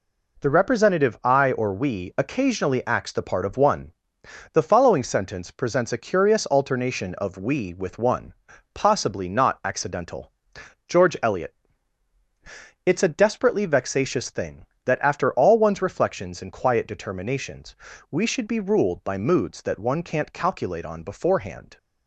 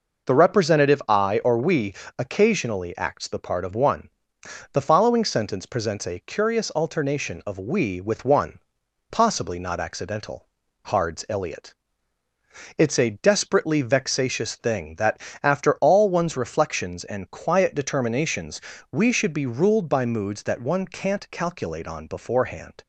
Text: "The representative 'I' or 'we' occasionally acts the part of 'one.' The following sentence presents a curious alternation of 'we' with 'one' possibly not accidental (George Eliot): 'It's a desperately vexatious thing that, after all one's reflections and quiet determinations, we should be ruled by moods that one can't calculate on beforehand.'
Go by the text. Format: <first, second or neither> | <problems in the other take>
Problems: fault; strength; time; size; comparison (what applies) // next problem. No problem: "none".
first | pauses between "we" and "occasionally"; slight; at 1.9 s; 0.20 s long // pauses between "one" and "possibly"; noticeable; at 8.5 s; 0.50 s long; also in the first // says "Hards" for "George"; at 10.8 s